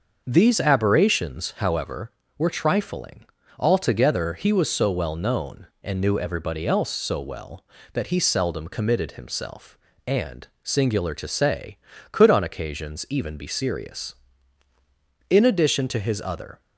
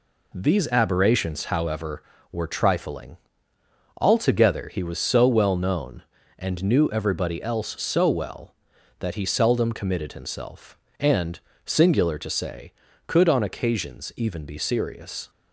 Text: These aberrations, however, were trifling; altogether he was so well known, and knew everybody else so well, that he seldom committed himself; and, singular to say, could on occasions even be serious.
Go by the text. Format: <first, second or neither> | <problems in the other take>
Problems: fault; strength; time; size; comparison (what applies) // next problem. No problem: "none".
second | starts louder than the rest; noticeable; until 1.2 s; 6 dB // goes on to say "In addition to his other"; from 15.2 s on; 1.3 s long